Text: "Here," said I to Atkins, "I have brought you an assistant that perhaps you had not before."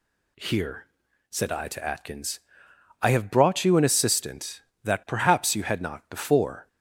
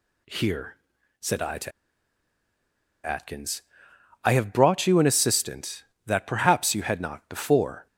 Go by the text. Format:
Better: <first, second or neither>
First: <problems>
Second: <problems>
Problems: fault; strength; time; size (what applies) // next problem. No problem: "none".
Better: first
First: none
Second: pauses between "to" and "Atkins"; strong; at 1.7 s; 1.3 s long